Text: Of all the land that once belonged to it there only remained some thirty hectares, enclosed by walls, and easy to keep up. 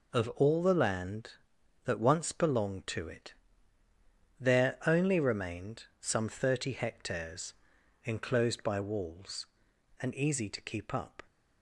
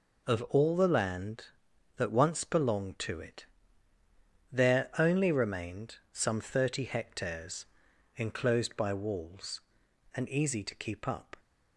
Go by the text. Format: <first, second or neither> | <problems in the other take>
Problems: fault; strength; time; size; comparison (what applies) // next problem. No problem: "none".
neither | pauses between "it" and "there"; the same in both // pauses between "remained" and "some"; slight; the same in both